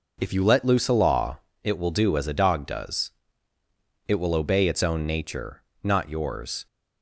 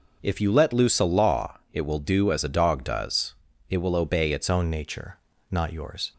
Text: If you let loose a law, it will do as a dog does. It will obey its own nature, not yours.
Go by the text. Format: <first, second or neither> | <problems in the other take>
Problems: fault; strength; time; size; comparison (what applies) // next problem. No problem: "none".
first | changes voice at "own"; from 4.4 s on; 1.7 s long